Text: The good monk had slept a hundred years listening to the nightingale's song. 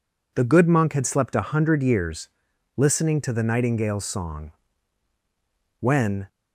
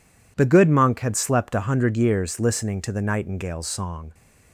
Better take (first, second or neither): second